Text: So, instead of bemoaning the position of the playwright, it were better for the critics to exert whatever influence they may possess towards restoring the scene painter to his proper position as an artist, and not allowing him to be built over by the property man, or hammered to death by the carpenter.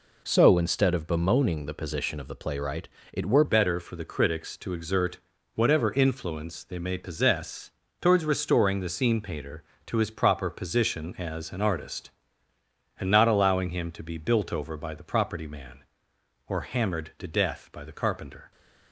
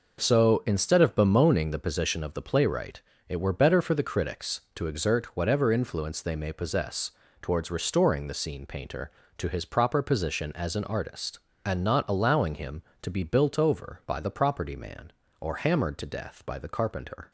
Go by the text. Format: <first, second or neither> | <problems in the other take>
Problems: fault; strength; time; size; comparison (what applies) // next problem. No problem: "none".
second | changes voice at "better"; from 3.4 s on; 15.1 s long // pauses between "exert" and "whatever"; slight; at 5.1 s; 0.36 s long // pauses between "possess" and "towards"; slight; at 7.7 s; 0.30 s long; slight in the second